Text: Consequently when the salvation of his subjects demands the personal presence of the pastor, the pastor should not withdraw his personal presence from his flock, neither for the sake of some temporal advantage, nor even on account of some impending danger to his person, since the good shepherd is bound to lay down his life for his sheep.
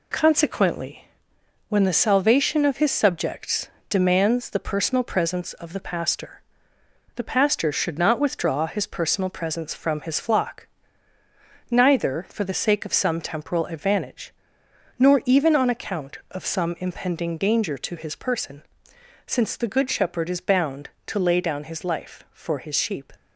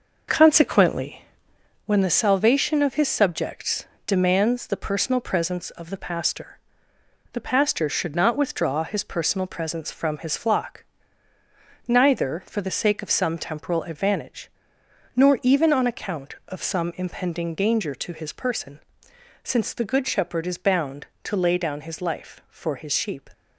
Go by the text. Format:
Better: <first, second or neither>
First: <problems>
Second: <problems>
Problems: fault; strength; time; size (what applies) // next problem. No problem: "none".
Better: first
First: pauses between "Consequently" and "when"; noticeable; at 1.0 s; 0.64 s long // pauses between "subjects" and "demands"; slight; at 3.6 s; 0.20 s long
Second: starts louder than the rest; noticeable; until 2.0 s; 5.5 dB // pauses between "Consequently" and "when"; noticeable; at 1.2 s; 0.64 s long // pauses between "subjects" and "demands"; slight; at 3.8 s; 0.20 s long